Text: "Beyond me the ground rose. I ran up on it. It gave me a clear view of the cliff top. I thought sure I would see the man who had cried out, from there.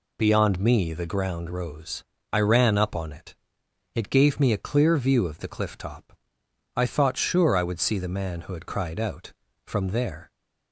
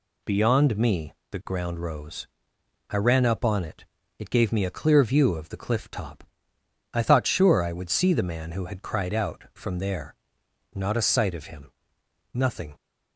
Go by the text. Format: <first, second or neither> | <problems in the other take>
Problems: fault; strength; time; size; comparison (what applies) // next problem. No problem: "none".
first | pauses between "me" and "the"; slight; at 1.1 s; 0.18 s long // goes on to say "Not a sight of him Nothing"; strong; from 10.7 s on; 2.0 s long